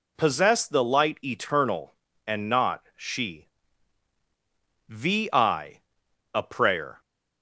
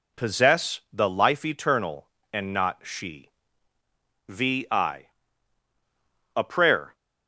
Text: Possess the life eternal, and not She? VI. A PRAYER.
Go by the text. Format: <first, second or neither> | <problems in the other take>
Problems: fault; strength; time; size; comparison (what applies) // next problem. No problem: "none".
second | says "light" for "life"; at 0.8 s